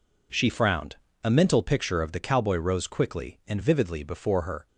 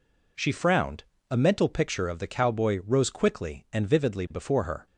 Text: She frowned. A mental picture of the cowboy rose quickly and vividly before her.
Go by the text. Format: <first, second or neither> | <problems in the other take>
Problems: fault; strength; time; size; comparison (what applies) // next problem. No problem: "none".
neither | none